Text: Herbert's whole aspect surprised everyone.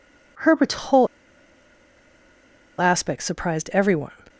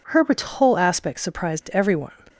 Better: second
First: pauses between "whole" and "aspect"; strong; at 1.0 s; 1.7 s long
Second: none

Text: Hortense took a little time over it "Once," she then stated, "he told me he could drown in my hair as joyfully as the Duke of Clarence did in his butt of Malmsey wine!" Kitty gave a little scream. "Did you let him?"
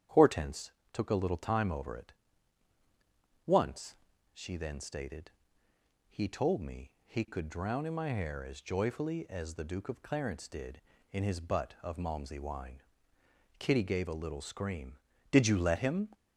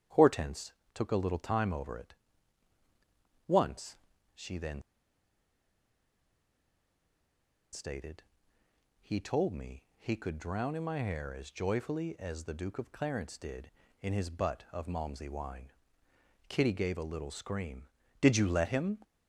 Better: first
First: starts louder than the rest; strong; until 1.3 s; 9.5 dB // pauses between "Hortense" and "took"; slight; at 0.7 s; 0.20 s long // pauses between "it" and "Once"; strong; at 2.1 s; 1.3 s long // pauses between "me" and "he"; slight; at 6.8 s; 0.16 s long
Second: starts louder than the rest; strong; until 1.3 s; 9.5 dB // pauses between "Hortense" and "took"; slight; at 0.7 s; 0.20 s long // pauses between "it" and "Once"; strong; at 2.1 s; 1.3 s long // pauses between "then" and "stated"; strong; at 4.8 s; 2.9 s long // pauses between "me" and "he"; slight; at 9.8 s; 0.16 s long

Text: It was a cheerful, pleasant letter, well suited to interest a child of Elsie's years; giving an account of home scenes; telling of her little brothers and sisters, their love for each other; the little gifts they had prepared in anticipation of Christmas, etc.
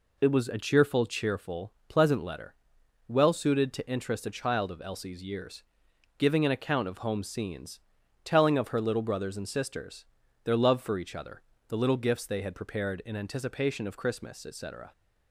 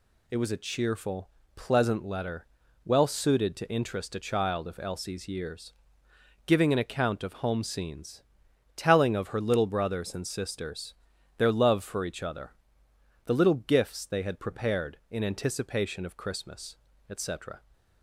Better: second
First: says "cheerful" twice; at 1.0 s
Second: none

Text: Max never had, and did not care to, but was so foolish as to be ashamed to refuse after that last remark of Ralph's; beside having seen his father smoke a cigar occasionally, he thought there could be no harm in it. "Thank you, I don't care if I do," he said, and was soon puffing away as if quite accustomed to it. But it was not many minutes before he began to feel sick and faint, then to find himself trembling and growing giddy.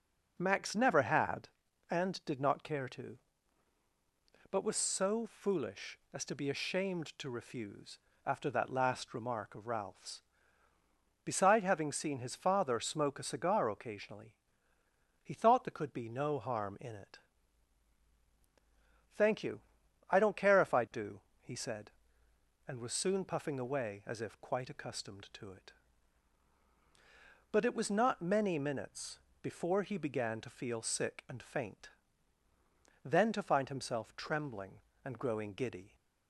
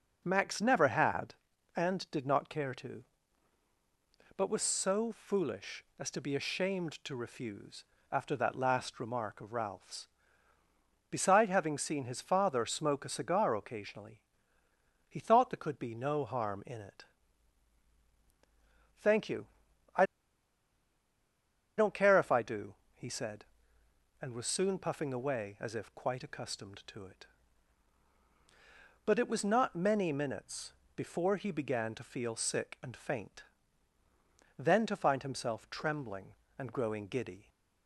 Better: first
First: pauses between "refuse" and "after"; slight; at 7.9 s; 0.28 s long // pauses between "minutes" and "before"; slight; at 29.1 s; 0.24 s long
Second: pauses between "refuse" and "after"; slight; at 7.8 s; 0.28 s long // pauses between "I" and "don't"; strong; at 20.0 s; 1.7 s long // pauses between "minutes" and "before"; slight; at 30.7 s; 0.24 s long

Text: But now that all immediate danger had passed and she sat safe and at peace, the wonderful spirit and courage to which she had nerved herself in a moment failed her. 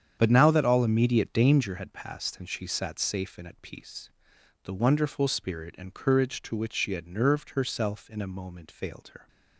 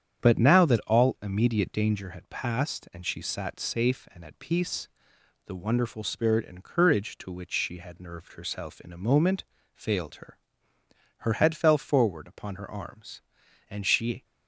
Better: first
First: starts louder than the rest; strong; until 1.1 s; 8.5 dB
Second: starts louder than the rest; strong; until 1.2 s; 8.5 dB // pauses between "moment" and "failed"; slight; at 9.4 s; 0.30 s long // goes on to say "Her head fell forward upon her arms and she"; strong; from 11.1 s on; 3.0 s long

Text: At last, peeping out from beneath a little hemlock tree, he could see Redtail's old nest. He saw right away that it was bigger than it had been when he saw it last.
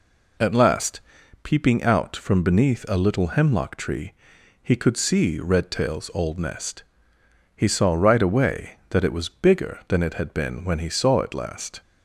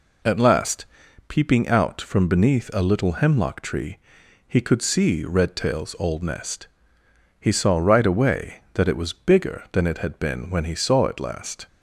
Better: neither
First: none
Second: none

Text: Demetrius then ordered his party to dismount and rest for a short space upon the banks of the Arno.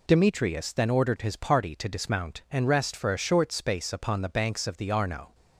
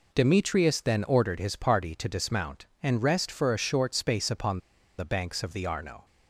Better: first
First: none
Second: pauses between "upon" and "the"; at 4.5 s; 0.39 s long

